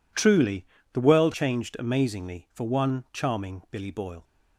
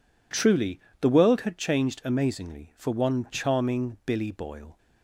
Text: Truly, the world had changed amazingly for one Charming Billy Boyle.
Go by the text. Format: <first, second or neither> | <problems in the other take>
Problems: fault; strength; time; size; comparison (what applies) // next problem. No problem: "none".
second | skips "had"; at 1.3 s